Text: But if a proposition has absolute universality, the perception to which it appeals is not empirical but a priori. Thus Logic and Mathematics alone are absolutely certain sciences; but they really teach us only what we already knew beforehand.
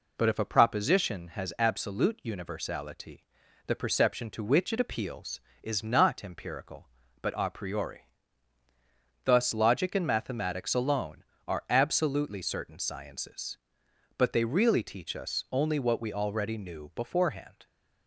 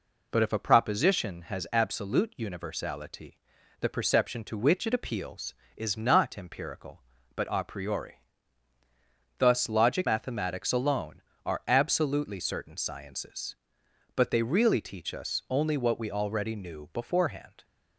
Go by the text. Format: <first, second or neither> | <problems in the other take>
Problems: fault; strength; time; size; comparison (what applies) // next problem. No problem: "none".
first | skips "and"; at 10.0 s